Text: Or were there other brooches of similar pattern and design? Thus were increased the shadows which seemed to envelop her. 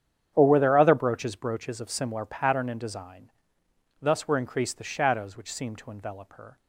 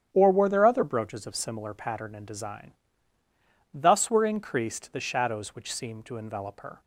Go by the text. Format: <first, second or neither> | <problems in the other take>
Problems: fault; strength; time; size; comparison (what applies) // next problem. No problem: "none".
second | starts louder than the rest; strong; until 1.3 s; 8.5 dB; strong in the second // says "brooches" twice; at 1.3 s